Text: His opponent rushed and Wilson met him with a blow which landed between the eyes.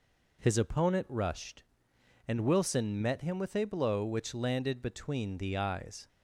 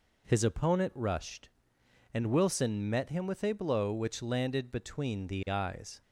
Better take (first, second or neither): neither